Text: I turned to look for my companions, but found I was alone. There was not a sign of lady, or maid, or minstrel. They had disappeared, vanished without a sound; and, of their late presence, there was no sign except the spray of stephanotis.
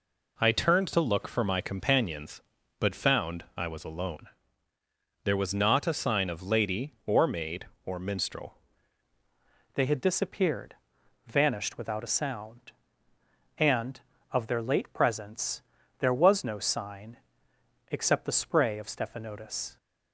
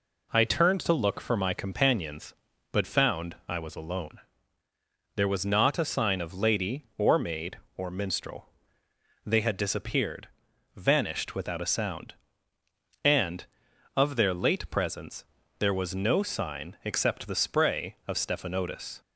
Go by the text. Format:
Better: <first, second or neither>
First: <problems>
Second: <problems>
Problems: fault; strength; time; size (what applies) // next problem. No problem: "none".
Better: second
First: changes voice at "They"; from 9.7 s on; 10.0 s long // pauses between "sign" and "except"; noticeable; at 17.1 s; 0.72 s long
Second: none